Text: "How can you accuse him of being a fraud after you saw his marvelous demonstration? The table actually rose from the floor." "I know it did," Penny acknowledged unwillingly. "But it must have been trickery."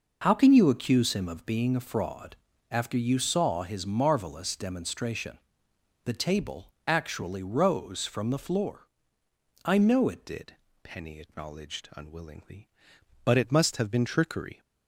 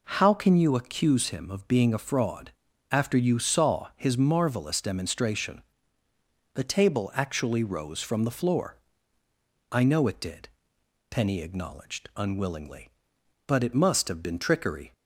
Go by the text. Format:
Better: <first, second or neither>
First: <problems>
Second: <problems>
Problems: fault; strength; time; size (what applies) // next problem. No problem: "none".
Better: second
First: pauses between "fraud" and "after"; slight; at 2.3 s; 0.34 s long // pauses between "table" and "actually"; slight; at 6.7 s; 0.16 s long // changes voice at "did"; from 10.2 s on; 4.3 s long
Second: pauses between "fraud" and "after"; at 2.5 s; 0.40 s long